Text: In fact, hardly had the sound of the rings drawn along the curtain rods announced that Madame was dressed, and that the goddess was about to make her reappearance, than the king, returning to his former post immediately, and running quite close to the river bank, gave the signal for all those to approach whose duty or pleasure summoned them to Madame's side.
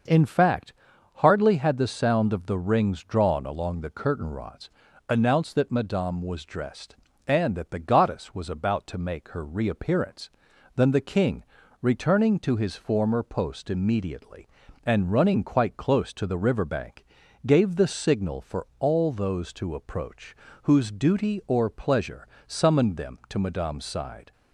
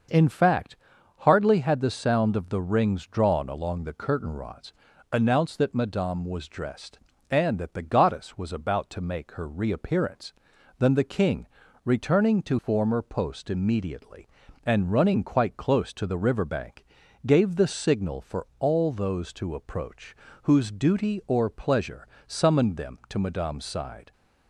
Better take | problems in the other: first | starts louder than the rest; until 1.5 s; 6.5 dB; also in the first // pauses between "rods" and "announced"; at 4.7 s; 0.38 s long; also in the first // skips "his"; at 12.5 s // pauses between "approach" and "whose"; slight; at 20.1 s; 0.28 s long; slight in the first // pauses between "pleasure" and "summoned"; slight; at 22.0 s; 0.18 s long; slight in the first

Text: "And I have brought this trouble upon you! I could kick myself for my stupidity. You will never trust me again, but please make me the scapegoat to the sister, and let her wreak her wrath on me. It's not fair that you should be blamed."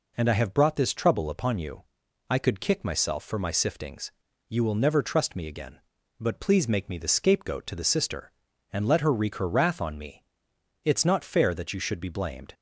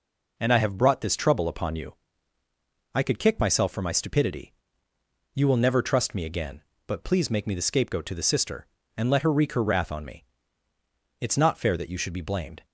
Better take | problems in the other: second | says "siftings" for "stupidity"; at 3.4 s

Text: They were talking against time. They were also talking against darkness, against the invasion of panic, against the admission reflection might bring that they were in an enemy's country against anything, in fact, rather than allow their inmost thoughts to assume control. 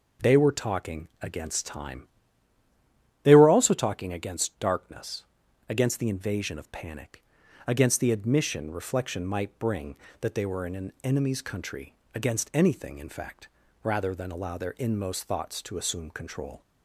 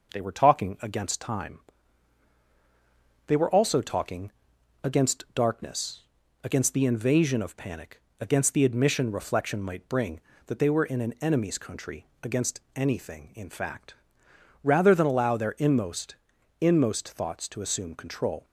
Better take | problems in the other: first | pauses between "talking" and "against"; noticeable; at 4.3 s; 0.50 s long // pauses between "country" and "against"; slight; at 12.0 s; 0.16 s long; slight in the first // says "inmost" twice; at 16.6 s

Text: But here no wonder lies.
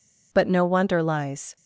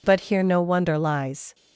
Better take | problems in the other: second | skips "here"; at 0.4 s

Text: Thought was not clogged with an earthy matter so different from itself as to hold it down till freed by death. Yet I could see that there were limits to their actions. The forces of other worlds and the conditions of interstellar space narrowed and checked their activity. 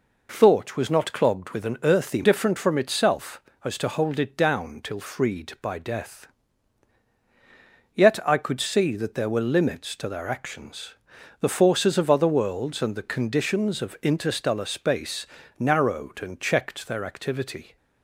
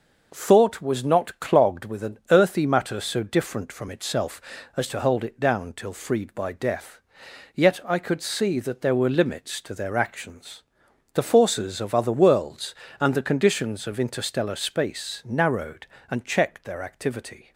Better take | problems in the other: second | skips "matter so"; at 2.2 s // pauses between "space" and "narrowed"; slight; at 15.2 s; 0.32 s long

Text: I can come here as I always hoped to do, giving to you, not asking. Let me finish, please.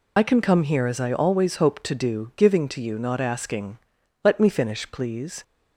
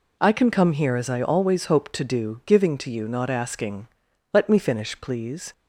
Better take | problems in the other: second | loses the start of "I"; at 0.1 s; 55 ms

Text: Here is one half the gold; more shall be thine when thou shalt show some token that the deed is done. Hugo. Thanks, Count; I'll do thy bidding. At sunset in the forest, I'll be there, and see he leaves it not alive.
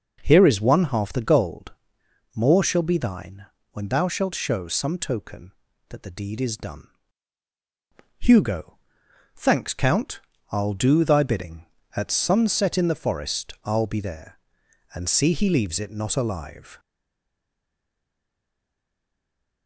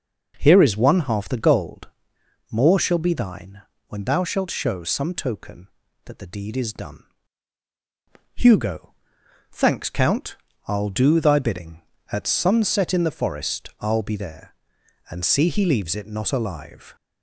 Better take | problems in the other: second | pauses between "thine" and "when"; slight; at 3.4 s; 0.26 s long; slight in the second // stays silent after the last word; strong; from 16.7 s on; 2.9 s long

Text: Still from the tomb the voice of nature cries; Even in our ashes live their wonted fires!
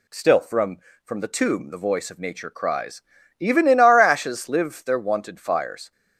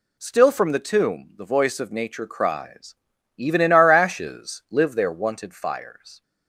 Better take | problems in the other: second | says "from" twice; at 1.0 s

